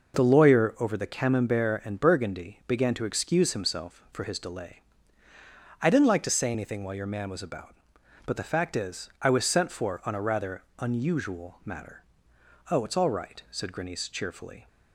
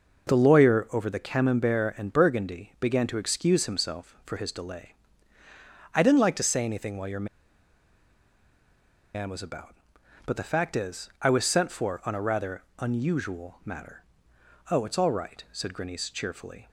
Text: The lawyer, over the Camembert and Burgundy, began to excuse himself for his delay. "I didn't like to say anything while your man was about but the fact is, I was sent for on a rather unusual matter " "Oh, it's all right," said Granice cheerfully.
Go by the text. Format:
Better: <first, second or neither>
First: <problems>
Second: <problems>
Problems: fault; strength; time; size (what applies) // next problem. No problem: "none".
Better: first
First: pauses between "rather" and "unusual"; slight; at 10.6 s; 0.16 s long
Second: pauses between "your" and "man"; strong; at 7.2 s; 1.8 s long // pauses between "rather" and "unusual"; slight; at 12.6 s; 0.16 s long